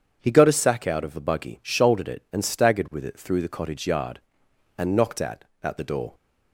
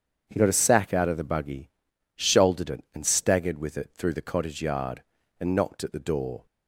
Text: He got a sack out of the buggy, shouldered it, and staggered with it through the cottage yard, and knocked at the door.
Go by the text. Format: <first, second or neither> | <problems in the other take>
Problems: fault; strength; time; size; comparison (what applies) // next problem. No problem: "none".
second | starts louder than the rest; strong; until 1.2 s; 7.5 dB; strong in the second // says "at" twice; at 5.6 s